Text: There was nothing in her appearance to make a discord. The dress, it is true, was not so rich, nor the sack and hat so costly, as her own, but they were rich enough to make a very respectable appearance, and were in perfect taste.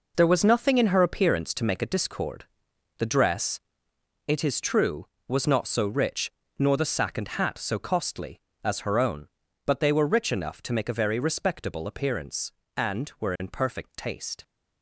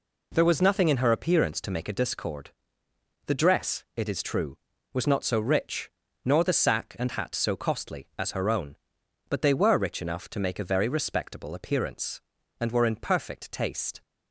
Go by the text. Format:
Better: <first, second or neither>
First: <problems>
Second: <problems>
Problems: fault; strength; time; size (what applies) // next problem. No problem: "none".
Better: second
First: gets quieter; strong; throughout; 10 dB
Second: none